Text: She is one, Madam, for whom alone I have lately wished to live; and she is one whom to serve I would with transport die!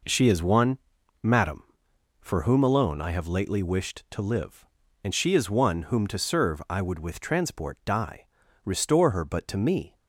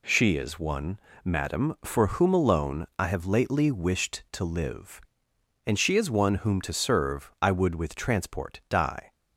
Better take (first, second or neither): second